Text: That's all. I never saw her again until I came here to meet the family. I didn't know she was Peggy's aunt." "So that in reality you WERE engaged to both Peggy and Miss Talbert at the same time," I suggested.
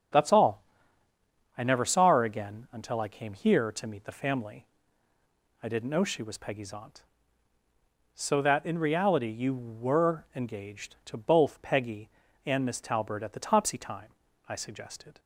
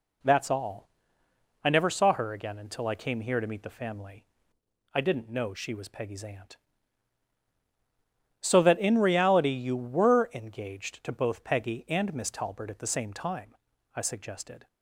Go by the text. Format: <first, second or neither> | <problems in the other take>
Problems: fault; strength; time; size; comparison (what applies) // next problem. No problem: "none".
second | starts louder than the rest; strong; until 2.0 s; 7.5 dB // says "topsy" for "same"; at 13.3 s